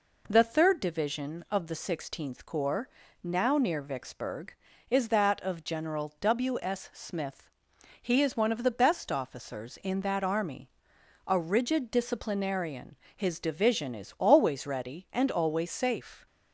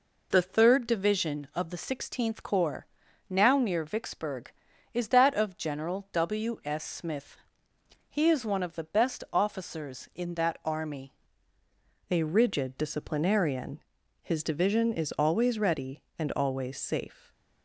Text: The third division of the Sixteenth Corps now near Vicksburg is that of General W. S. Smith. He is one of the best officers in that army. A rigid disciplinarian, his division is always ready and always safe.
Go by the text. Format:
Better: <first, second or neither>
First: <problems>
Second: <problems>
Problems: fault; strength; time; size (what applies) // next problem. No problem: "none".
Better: first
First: pauses between "Corps" and "now"; slight; at 2.8 s; 0.34 s long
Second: pauses between "Corps" and "now"; at 2.8 s; 0.42 s long // changes voice at "A"; from 12.0 s on; 5.3 s long